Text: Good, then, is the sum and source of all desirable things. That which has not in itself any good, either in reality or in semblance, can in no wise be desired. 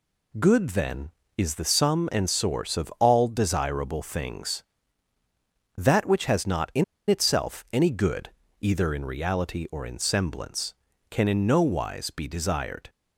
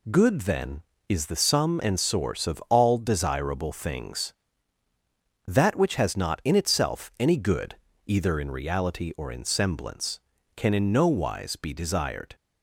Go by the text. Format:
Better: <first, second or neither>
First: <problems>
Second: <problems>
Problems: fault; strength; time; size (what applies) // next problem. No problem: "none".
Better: second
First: pauses between "in" and "itself"; slight; at 6.8 s; 0.24 s long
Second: none